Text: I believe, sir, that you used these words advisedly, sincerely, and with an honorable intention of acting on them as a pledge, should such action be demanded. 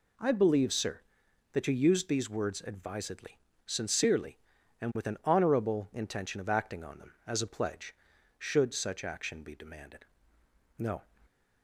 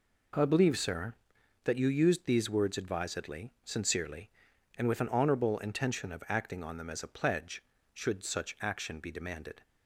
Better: second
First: goes on to say "No"; slight; from 10.7 s on; 0.26 s long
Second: none

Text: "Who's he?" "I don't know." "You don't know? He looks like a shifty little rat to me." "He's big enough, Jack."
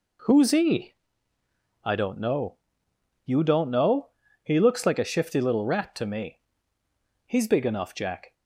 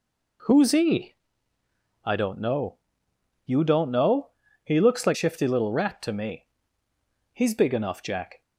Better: first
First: none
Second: skips "a"; at 5.1 s

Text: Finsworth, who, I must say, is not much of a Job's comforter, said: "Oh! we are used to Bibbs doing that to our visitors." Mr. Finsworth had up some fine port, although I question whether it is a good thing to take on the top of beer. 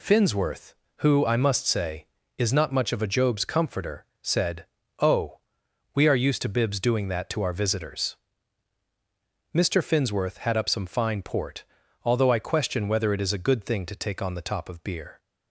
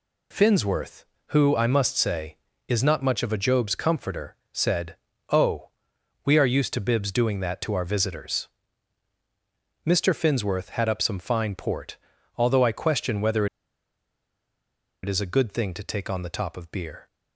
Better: first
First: none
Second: pauses between "whether" and "it"; strong; at 13.4 s; 1.5 s long

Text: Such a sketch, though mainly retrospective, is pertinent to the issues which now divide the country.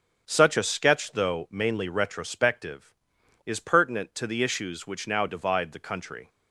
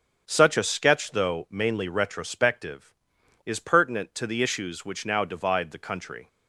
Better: neither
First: starts louder than the rest; strong; until 1.2 s; 7.5 dB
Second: starts louder than the rest; strong; until 1.2 s; 8 dB

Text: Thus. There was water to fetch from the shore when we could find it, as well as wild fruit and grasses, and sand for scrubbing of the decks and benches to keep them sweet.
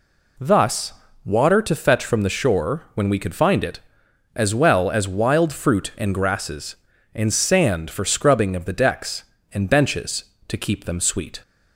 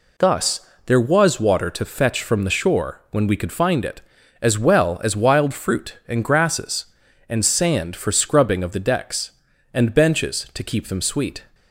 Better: second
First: skips "There was"; at 1.0 s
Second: none

